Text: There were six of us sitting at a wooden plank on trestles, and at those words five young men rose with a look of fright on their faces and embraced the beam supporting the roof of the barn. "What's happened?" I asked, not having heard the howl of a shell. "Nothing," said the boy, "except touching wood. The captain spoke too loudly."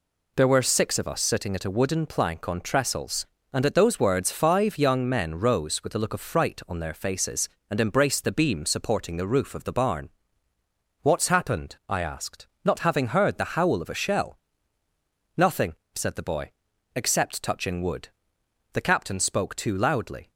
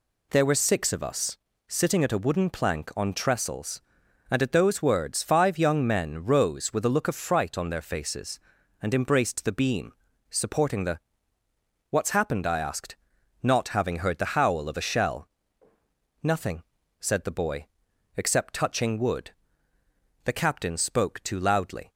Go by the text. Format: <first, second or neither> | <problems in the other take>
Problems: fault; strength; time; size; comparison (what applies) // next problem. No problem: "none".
first | pauses between "us" and "sitting"; slight; at 1.3 s; 0.32 s long // pauses between "beam" and "supporting"; slight; at 9.9 s; 0.36 s long // skips "roof of the barn"; at 11.4 s